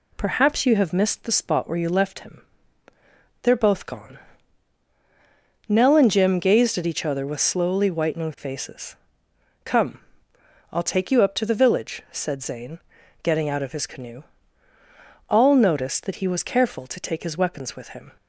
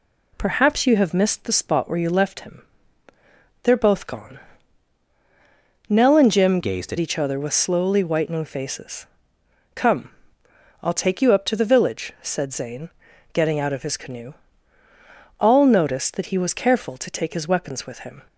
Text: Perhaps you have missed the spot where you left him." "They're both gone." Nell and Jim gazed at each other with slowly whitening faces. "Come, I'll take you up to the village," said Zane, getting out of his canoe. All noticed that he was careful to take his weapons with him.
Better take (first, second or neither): first